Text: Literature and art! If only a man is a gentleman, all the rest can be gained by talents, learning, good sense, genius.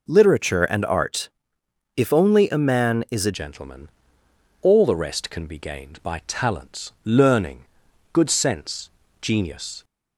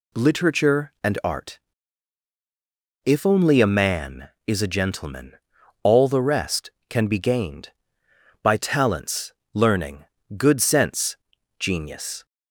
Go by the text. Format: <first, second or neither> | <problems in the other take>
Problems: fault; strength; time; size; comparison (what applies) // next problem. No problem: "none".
second | changes voice at "gentleman"; from 3.3 s on; 6.5 s long